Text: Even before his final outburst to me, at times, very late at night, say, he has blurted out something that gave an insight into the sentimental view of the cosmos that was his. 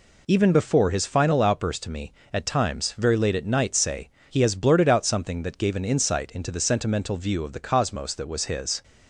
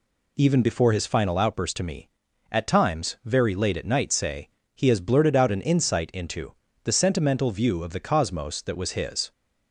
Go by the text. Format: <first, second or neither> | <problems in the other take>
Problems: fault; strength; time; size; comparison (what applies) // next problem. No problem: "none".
first | skips "something that gave"; at 5.5 s // pauses between "into" and "the"; slight; at 6.5 s; 0.30 s long